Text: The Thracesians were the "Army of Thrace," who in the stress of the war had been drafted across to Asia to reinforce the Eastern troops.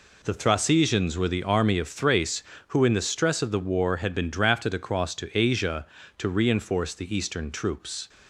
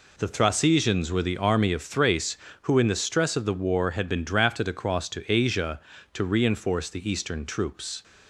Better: neither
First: none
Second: none

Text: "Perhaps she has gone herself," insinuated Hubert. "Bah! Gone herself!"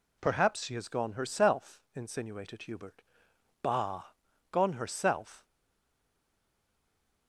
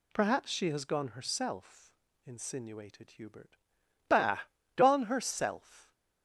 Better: second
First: stays silent after the last word; noticeable; from 5.4 s on; 1.8 s long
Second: none

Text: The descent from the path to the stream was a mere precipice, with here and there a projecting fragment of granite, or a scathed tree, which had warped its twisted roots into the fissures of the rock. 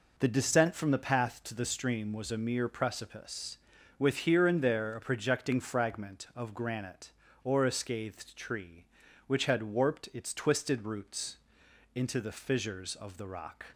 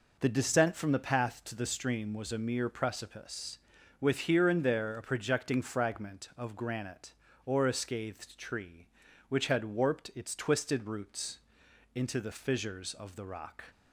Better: neither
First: pauses between "roots" and "into"; noticeable; at 11.3 s; 0.58 s long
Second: pauses between "roots" and "into"; noticeable; at 11.3 s; 0.56 s long

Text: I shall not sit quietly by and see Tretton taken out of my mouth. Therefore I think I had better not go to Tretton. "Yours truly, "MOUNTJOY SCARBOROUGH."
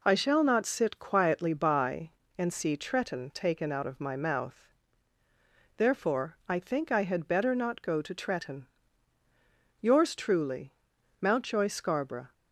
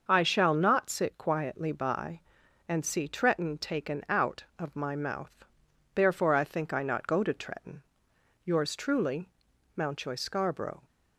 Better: first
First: none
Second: starts louder than the rest; until 1.0 s; 6.5 dB // skips "had better"; at 6.8 s

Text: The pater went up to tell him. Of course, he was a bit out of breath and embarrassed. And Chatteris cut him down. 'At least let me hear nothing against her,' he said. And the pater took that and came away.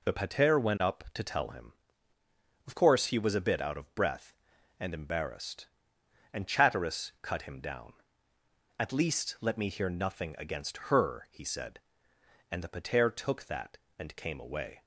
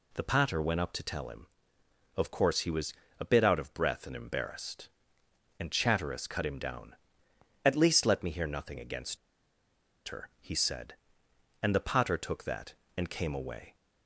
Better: first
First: none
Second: pauses between "was" and "a"; slight; at 2.9 s; 0.26 s long // pauses between "against" and "her"; noticeable; at 9.1 s; 0.90 s long

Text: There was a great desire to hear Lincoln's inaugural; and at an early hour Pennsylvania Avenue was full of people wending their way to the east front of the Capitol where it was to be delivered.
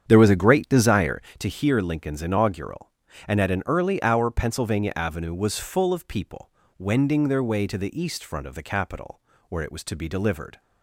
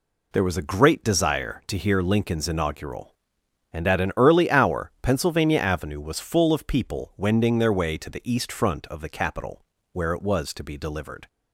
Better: second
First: starts louder than the rest; strong; until 1.2 s; 8 dB // pauses between "people" and "wending"; slight; at 6.4 s; 0.28 s long // pauses between "Capitol" and "where"; slight; at 9.2 s; 0.26 s long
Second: pauses between "Capitol" and "where"; slight; at 9.6 s; 0.26 s long

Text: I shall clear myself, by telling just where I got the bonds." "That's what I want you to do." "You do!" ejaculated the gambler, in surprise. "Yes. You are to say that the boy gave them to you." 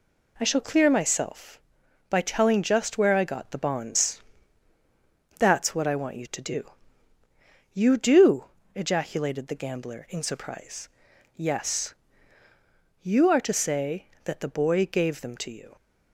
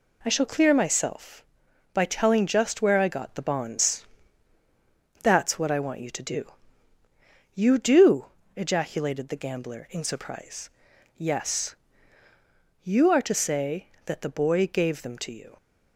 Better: neither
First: none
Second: none

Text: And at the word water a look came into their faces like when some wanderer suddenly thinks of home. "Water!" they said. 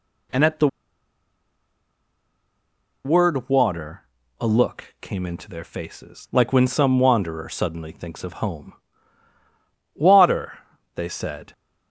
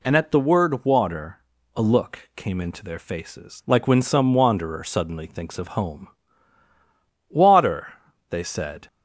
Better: second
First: pauses between "the" and "word"; strong; at 0.6 s; 2.3 s long // pauses between "water" and "a"; at 4.0 s; 0.38 s long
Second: pauses between "water" and "a"; at 1.3 s; 0.38 s long

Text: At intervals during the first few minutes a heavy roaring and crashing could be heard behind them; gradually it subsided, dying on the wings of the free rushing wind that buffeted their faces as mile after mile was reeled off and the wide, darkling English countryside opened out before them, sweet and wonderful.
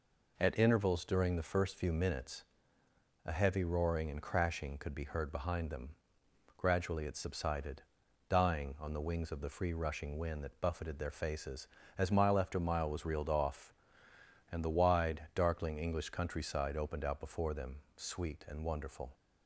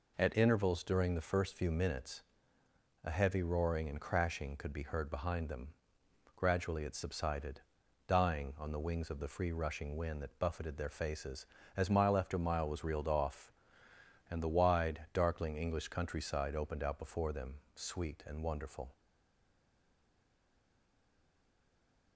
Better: first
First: pauses between "minutes" and "a"; noticeable; at 2.4 s; 0.82 s long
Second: pauses between "minutes" and "a"; noticeable; at 2.2 s; 0.82 s long // stays silent after the last word; strong; from 18.9 s on; 3.2 s long

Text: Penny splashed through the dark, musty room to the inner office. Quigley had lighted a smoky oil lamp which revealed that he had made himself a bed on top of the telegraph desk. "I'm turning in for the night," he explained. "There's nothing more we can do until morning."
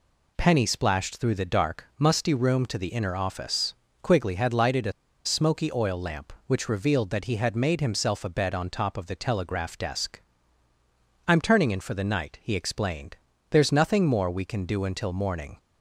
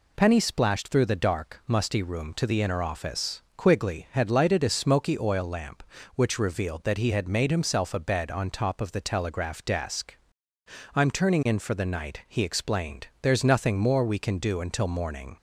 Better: second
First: pauses between "a" and "smoky"; slight; at 4.9 s; 0.33 s long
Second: none

